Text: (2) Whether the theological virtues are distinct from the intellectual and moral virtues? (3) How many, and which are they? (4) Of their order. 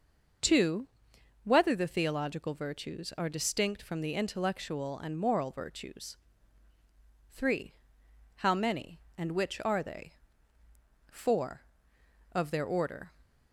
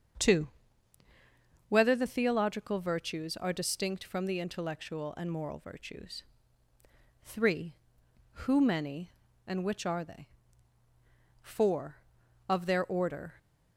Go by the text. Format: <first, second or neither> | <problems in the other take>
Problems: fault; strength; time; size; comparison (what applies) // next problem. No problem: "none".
first | starts louder than the rest; until 2.3 s; 7 dB // says "Who" for "How"; at 8.3 s